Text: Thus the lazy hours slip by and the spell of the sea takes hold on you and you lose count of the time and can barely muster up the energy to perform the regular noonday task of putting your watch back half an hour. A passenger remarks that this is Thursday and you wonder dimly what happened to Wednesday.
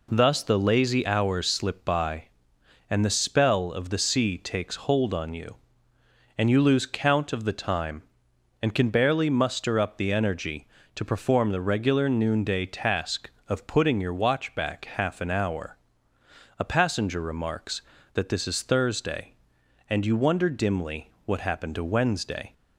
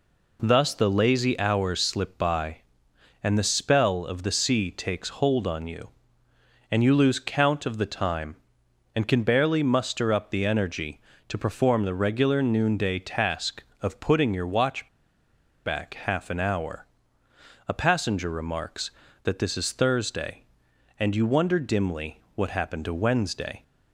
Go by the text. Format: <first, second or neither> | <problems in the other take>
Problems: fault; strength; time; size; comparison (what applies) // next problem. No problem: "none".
first | pauses between "watch" and "back"; noticeable; at 14.8 s; 0.76 s long